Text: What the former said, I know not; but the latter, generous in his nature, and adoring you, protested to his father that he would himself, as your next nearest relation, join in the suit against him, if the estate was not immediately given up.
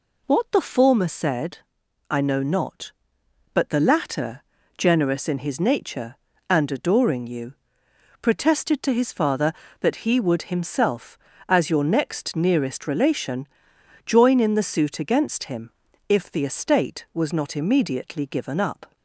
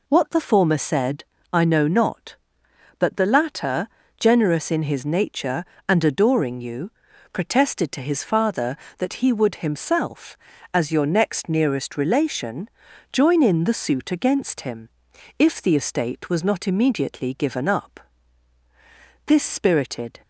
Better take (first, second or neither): first